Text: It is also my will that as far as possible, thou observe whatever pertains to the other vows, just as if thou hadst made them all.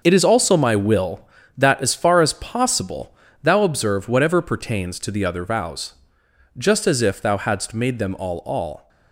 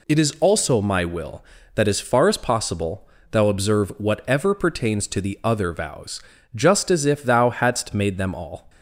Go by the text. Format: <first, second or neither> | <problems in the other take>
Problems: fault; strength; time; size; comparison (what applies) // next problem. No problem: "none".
second | starts louder than the rest; noticeable; until 1.0 s; 6 dB // says "all" twice; at 8.3 s